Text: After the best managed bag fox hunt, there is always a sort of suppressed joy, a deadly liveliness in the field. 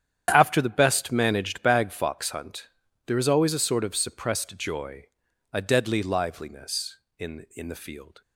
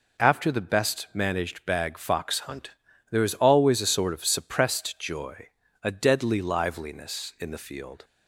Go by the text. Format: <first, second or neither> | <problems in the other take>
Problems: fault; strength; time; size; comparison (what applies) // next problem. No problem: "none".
second | starts louder than the rest; strong; until 1.3 s; 9.5 dB // says "in" twice; at 7.5 s